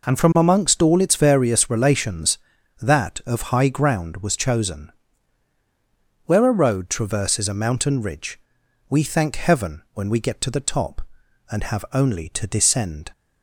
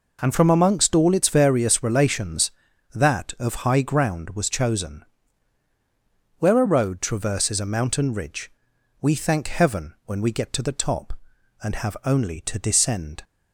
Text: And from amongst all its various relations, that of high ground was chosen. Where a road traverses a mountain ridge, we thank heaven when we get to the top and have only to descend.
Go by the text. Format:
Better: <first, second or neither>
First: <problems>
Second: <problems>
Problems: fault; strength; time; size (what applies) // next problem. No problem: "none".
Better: neither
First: none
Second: none